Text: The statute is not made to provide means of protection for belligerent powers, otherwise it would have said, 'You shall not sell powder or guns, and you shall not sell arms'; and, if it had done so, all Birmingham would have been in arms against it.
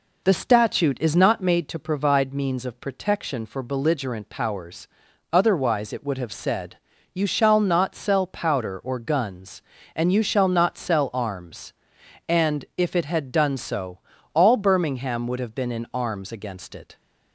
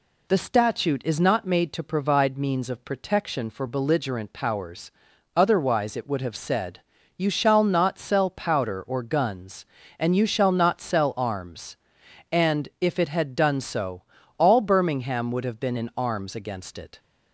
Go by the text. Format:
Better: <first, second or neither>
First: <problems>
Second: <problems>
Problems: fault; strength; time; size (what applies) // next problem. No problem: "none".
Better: second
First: starts louder than the rest; noticeable; until 1.6 s; 4.5 dB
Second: none